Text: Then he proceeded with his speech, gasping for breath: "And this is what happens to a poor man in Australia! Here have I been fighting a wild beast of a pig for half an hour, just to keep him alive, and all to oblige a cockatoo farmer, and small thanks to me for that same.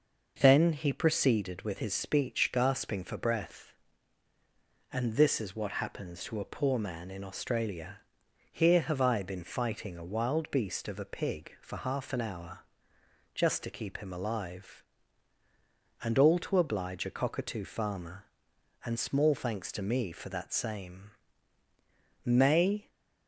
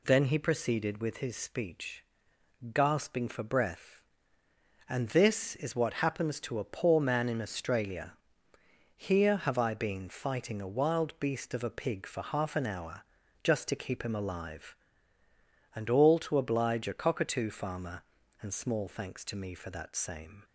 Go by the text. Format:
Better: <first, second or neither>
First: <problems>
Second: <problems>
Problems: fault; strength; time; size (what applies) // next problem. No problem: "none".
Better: second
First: goes on to say "May"; noticeable; from 22.2 s on; 0.66 s long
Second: none